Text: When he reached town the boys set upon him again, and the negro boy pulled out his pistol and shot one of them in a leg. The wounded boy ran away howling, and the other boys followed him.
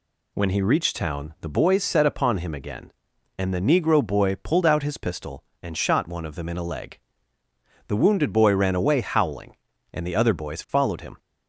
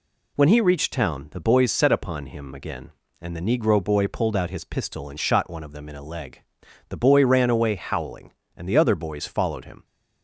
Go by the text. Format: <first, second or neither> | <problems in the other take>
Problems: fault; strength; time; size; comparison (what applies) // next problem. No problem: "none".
first | skips "wounded"; at 6.9 s